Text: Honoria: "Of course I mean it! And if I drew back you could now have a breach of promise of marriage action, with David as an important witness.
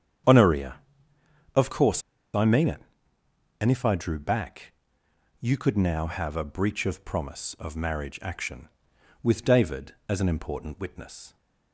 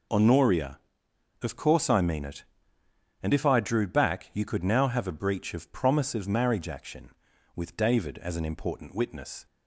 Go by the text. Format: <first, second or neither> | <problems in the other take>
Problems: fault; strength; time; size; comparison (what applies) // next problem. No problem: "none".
second | starts louder than the rest; strong; until 2.3 s; 8.5 dB // pauses between "course" and "I"; slight; at 2.0 s; 0.32 s long // pauses between "back" and "you"; noticeable; at 4.7 s; 0.66 s long